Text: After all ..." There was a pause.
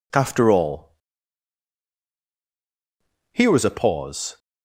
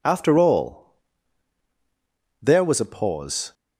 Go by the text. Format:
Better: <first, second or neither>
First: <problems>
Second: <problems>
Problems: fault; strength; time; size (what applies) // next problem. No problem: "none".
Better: second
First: says "Here" for "There"; at 3.3 s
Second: none